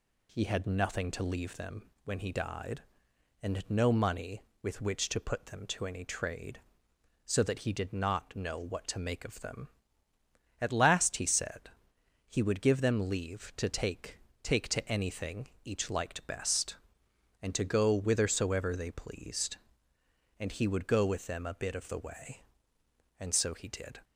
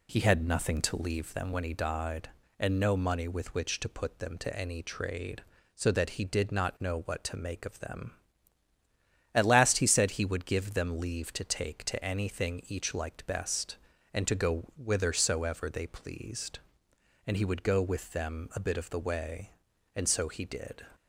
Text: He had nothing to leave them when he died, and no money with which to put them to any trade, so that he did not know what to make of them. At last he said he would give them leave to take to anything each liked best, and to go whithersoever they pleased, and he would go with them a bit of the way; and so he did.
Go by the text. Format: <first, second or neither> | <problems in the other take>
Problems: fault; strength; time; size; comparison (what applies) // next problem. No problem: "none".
second | pauses between "them" and "when"; slight; at 1.8 s; 0.18 s long // pauses between "said" and "he"; noticeable; at 11.6 s; 0.58 s long // says "take" twice; at 14.4 s // pauses between "anything" and "each"; slight; at 15.4 s; 0.16 s long